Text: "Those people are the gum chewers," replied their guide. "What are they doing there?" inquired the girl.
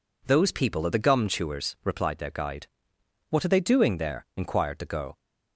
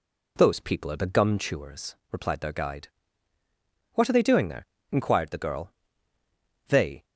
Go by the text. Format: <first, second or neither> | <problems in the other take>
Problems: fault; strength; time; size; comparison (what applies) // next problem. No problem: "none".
first | goes on to say "They"; slight; from 6.6 s on; 0.38 s long